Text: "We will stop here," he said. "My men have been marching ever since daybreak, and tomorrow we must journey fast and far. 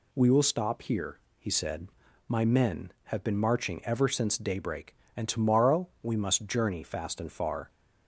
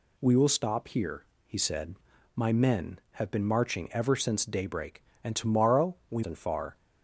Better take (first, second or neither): first